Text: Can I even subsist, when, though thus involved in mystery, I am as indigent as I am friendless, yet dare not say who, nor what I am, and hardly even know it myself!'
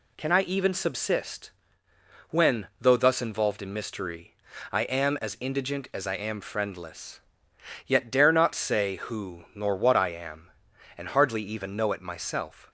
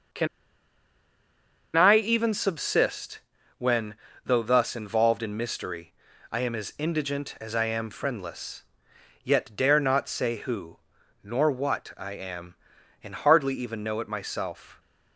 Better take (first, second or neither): first